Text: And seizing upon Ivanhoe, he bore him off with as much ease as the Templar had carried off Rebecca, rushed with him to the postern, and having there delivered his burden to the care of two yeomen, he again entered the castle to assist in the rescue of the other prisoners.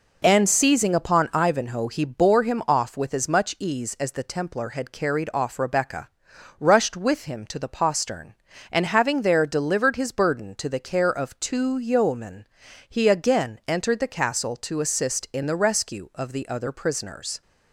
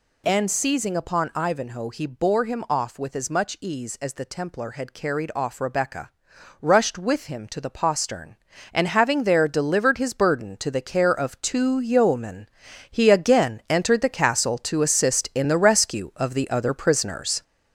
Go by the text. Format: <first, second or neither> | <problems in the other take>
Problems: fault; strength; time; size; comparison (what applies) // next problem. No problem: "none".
first | gets louder; noticeable; throughout; 5.5 dB